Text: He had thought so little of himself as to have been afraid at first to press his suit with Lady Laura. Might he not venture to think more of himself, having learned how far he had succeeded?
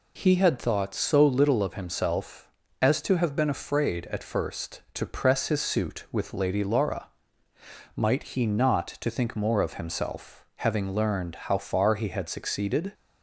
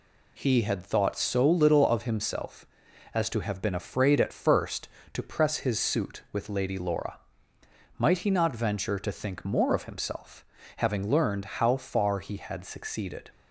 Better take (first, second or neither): second